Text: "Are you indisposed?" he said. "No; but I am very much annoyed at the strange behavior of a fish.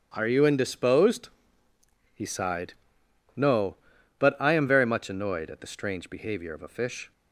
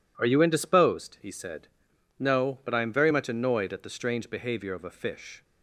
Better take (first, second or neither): second